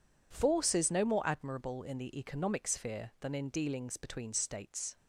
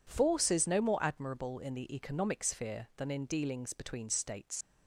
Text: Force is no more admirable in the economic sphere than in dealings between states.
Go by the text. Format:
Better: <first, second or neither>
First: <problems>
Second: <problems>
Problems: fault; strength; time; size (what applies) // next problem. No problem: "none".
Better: first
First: none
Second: leaves "states" unfinished; at 4.6 s; 110 ms